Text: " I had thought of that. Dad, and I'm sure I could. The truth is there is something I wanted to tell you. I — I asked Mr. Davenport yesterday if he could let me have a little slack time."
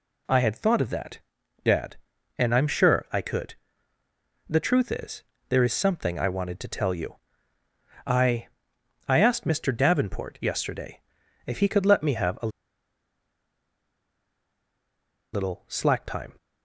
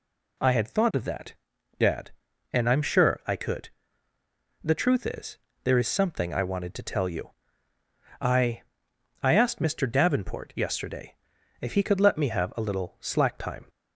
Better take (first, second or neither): second